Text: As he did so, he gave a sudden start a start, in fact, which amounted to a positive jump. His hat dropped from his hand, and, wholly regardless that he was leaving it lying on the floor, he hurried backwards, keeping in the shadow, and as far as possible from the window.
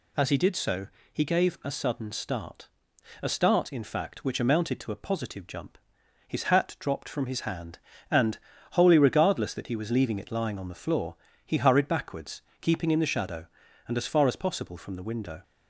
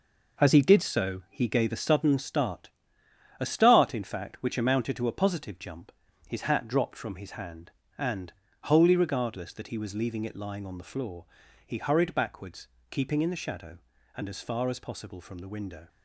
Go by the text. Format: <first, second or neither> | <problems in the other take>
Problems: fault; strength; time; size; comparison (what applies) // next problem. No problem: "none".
first | gets quieter; throughout; 7 dB // pauses between "start" and "a"; noticeable; at 2.6 s; 0.70 s long; noticeable in the first